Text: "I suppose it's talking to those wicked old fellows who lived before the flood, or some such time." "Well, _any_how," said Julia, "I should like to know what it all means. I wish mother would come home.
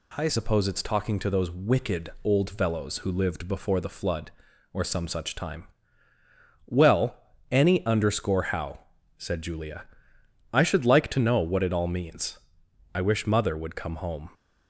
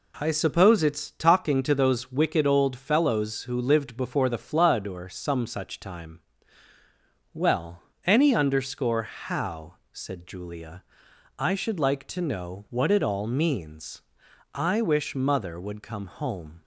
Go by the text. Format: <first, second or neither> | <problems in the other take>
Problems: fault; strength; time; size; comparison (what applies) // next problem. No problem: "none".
second | changes voice at "suppose"; from 0.2 s on; 14.0 s long